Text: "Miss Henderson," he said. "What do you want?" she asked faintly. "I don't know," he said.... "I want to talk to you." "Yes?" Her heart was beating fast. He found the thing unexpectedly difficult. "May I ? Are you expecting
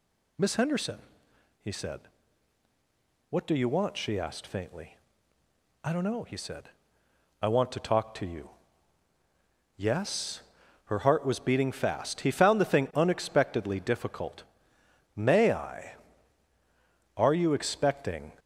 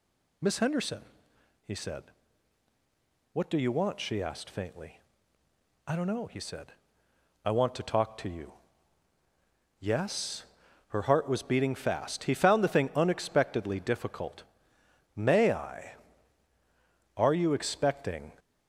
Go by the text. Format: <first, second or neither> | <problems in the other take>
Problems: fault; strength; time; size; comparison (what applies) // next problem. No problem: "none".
neither | none